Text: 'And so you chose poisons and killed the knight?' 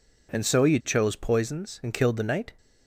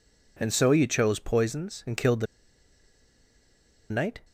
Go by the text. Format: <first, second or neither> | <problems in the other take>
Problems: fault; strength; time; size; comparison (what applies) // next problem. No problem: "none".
first | pauses between "the" and "knight"; strong; at 2.2 s; 1.6 s long